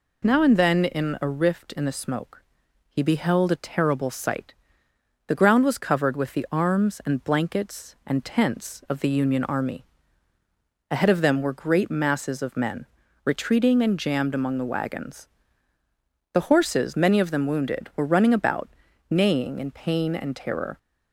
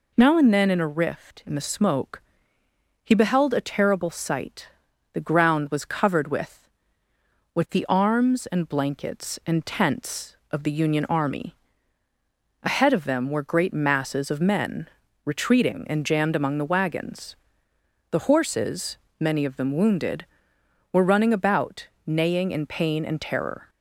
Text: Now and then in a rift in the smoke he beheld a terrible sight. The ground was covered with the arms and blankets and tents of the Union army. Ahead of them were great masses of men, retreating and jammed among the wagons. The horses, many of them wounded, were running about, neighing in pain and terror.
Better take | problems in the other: first | pauses between "smoke" and "he"; noticeable; at 2.2 s; 0.84 s long; also in the first // says "with" twice; at 7.5 s

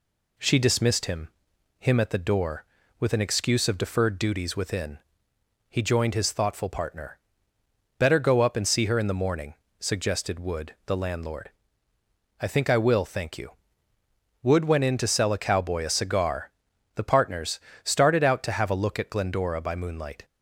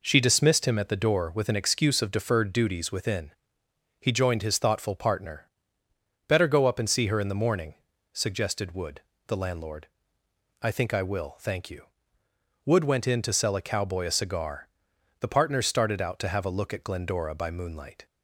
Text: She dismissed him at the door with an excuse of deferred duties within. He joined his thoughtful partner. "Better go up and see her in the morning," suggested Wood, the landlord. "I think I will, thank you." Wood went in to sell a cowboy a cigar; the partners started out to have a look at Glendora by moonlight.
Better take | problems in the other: second | says "him" twice; at 1.7 s // pauses between "partners" and "started"; slight; at 17.6 s; 0.24 s long

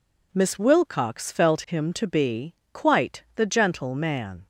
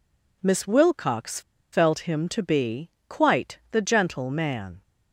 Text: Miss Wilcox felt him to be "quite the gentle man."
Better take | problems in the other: first | pauses between "Wilcox" and "felt"; slight; at 1.4 s; 0.32 s long // pauses between "be" and "quite"; slight; at 2.8 s; 0.18 s long; slight in the first

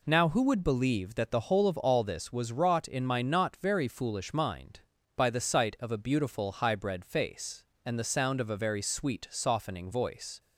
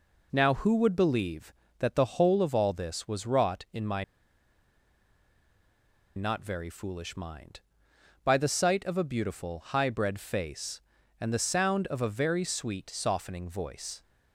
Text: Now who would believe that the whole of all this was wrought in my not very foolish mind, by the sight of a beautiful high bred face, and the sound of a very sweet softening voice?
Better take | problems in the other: first | pauses between "my" and "not"; strong; at 4.0 s; 2.1 s long

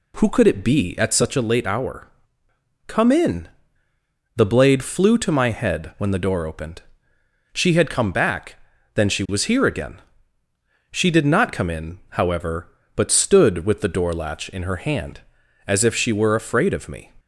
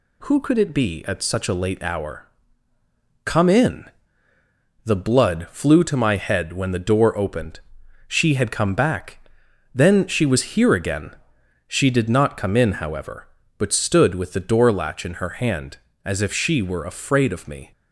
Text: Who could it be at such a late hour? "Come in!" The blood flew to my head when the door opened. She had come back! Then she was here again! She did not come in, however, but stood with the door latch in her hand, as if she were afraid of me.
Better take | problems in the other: second | says "blade" for "blood"; at 4.4 s

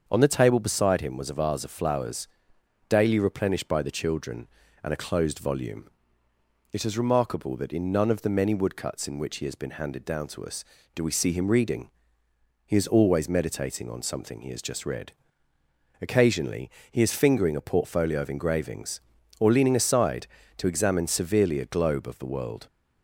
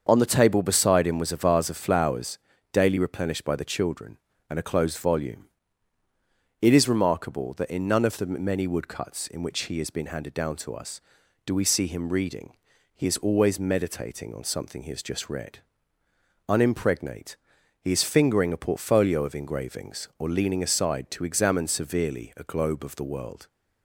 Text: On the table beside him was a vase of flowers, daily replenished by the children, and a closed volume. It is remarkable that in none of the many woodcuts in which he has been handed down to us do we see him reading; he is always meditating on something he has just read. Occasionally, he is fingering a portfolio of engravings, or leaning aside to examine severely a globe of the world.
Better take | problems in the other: first | starts louder than the rest; until 1.0 s; 6.5 dB; also in the first // says "Unimpregnate" for "Occasionally"; at 16.4 s

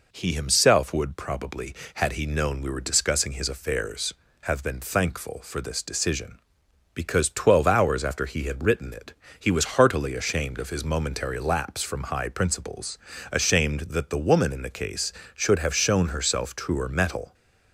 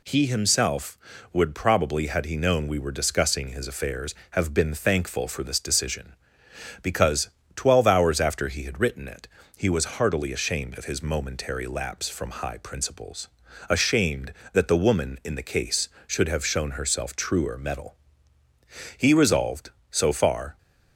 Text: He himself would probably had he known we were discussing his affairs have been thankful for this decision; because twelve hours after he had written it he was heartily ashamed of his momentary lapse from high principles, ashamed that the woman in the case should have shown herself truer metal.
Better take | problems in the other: first | pauses between "because" and "twelve"; slight; at 7.2 s; 0.26 s long // pauses between "it" and "he"; slight; at 9.2 s; 0.28 s long; slight in the first // goes on to say "He resolved so far"; from 18.9 s on; 1.6 s long

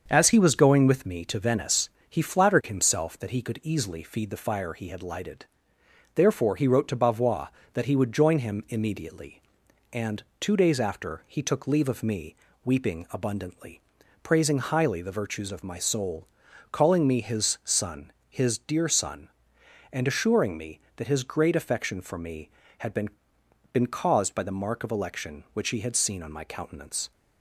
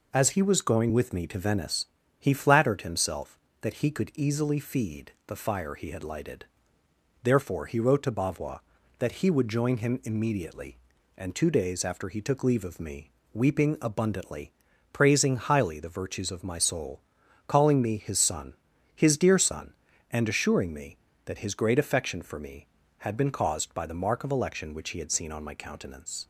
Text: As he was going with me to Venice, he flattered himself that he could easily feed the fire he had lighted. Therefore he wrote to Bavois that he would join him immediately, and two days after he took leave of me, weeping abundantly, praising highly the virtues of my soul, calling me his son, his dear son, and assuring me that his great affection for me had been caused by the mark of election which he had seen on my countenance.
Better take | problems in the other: second | starts louder than the rest; until 1.0 s; 7 dB // pauses between "and" and "two"; slight; at 10.2 s; 0.16 s long // says "been" twice; at 23.7 s

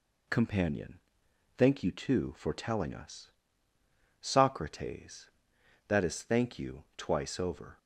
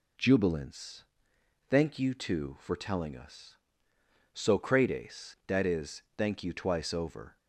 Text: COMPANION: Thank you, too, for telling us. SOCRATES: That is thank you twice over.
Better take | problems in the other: first | says "Jubilance" for "COMPANION"; at 0.1 s

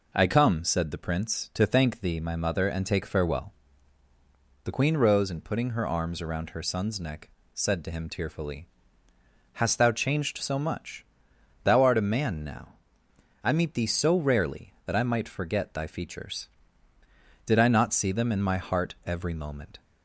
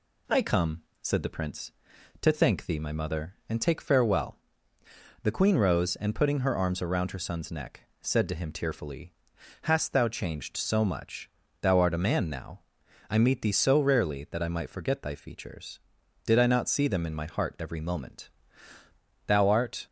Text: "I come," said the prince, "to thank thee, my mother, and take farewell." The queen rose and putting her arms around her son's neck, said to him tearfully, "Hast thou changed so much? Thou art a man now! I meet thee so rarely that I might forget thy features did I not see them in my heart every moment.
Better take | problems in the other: first | goes on to say "Thou art"; from 19.2 s on; 0.60 s long

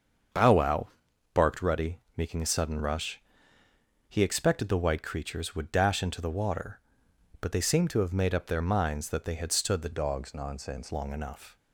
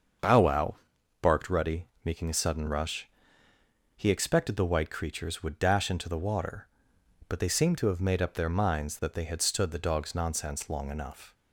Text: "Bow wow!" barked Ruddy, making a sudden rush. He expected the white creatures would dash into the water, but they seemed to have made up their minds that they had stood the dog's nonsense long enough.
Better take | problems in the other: second | starts louder than the rest; until 1.8 s; 7 dB; also in the second // changes voice from "dog's" to "nonsense"; from 9.9 to 10.9 s; 1.0 s long

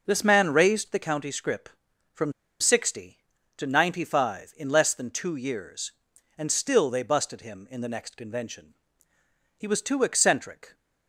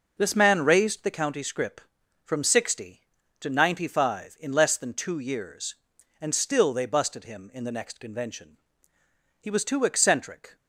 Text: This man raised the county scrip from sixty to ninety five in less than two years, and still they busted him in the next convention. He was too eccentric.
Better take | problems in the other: second | pauses between "from" and "sixty"; slight; at 2.3 s; 0.28 s long

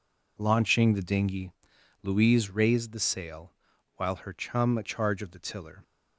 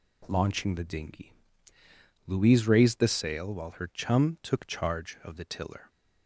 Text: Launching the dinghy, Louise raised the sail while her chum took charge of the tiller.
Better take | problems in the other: second | pauses between "sail" and "while"; at 3.5 s; 0.42 s long // skips "took"; at 4.8 s

